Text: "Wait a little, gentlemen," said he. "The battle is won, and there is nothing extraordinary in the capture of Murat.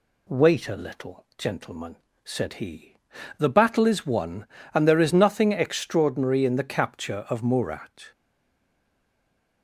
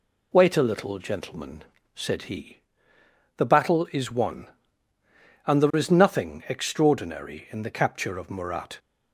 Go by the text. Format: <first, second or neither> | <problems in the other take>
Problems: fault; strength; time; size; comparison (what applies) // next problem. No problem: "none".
second | stays silent after the last word; noticeable; from 8.1 s on; 1.5 s long